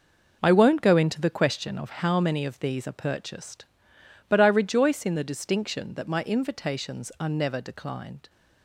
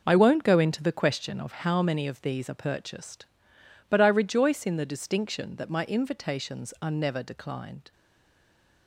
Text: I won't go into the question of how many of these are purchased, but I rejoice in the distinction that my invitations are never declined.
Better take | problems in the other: first | stays silent after the last word; slight; from 7.9 s on; 0.9 s long

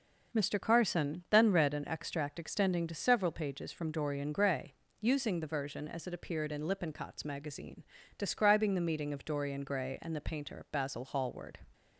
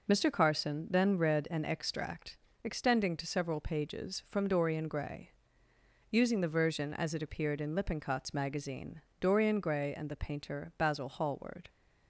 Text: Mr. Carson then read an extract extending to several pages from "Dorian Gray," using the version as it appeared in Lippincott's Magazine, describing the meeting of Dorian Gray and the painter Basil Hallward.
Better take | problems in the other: first | pauses between "extract" and "extending"; slight; at 2.3 s; 0.28 s long // skips "describing the meeting of"; at 9.1 s

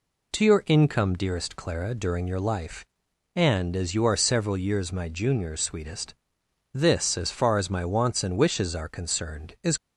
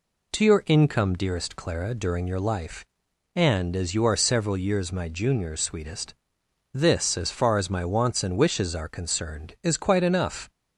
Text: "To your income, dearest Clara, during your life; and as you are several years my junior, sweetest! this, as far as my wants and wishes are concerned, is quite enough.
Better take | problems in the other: second | stops before "quite enough"; at 9.7 s

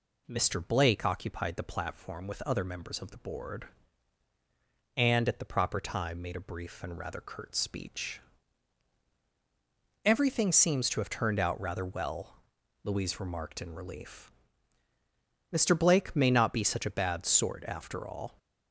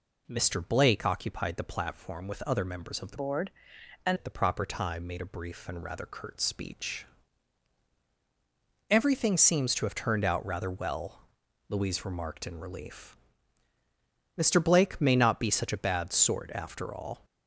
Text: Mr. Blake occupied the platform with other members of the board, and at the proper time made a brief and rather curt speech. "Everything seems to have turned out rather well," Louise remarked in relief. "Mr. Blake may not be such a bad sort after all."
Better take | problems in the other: first | changes voice from "board" to "and"; from 3.1 to 4.1 s; 1.0 s long

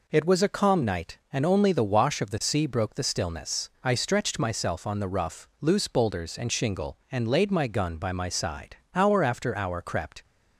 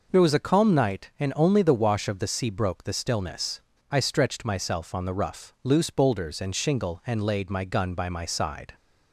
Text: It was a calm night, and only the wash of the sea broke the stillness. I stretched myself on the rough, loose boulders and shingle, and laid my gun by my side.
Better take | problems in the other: second | goes on to say "Hour after hour crept"; noticeable; from 8.9 s on; 1.2 s long

